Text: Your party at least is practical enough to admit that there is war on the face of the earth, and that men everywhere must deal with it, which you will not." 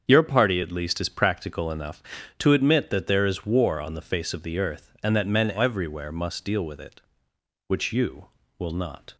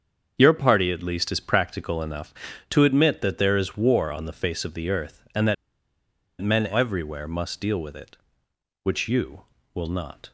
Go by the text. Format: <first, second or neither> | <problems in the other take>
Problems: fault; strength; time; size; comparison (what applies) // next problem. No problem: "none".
first | starts louder than the rest; strong; until 1.4 s; 7 dB; also in the first // pauses between "that" and "men"; noticeable; at 5.5 s; 0.86 s long